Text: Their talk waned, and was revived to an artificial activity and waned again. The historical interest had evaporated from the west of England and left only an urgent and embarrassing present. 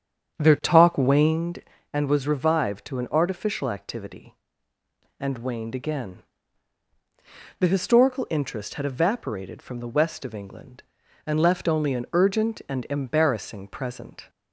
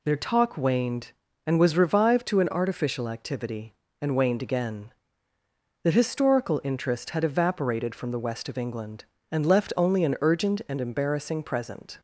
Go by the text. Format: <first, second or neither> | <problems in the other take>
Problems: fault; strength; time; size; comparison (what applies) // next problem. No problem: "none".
second | starts louder than the rest; strong; until 1.4 s; 8.5 dB